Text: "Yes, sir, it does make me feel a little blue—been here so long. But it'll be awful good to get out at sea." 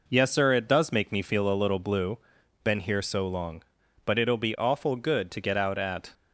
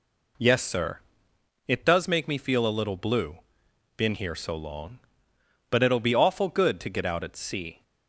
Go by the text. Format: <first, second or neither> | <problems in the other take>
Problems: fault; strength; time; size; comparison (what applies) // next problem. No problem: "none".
second | stops before "sea"; at 6.1 s